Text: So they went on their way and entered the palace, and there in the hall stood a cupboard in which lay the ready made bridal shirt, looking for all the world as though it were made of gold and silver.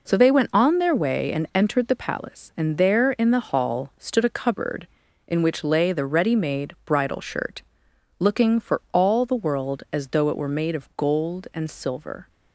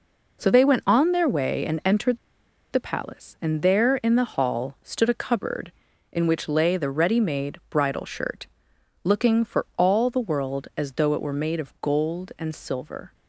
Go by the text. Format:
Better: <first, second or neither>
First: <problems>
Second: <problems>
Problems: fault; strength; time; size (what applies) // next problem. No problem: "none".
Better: first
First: none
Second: pauses between "entered" and "the"; noticeable; at 2.1 s; 0.54 s long